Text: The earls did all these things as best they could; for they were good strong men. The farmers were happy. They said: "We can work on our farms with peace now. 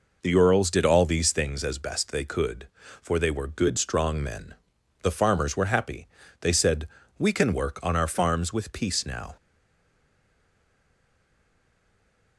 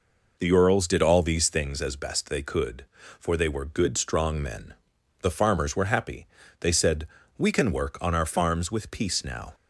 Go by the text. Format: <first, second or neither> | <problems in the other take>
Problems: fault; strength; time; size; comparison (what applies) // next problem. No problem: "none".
second | stays silent after the last word; strong; from 9.3 s on; 3.0 s long